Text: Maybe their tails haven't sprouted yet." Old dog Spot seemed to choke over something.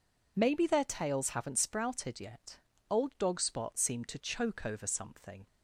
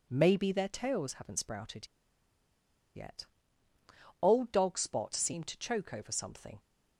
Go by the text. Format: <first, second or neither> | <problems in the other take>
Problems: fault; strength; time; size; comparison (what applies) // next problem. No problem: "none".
first | pauses between "sprouted" and "yet"; at 1.8 s; 1.0 s long